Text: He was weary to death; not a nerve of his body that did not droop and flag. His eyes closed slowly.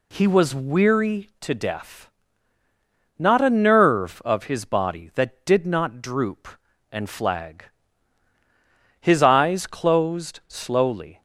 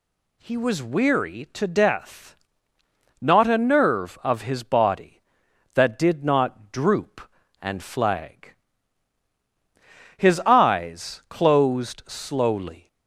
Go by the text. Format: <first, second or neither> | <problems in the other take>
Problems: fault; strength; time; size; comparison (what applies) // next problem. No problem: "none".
neither | none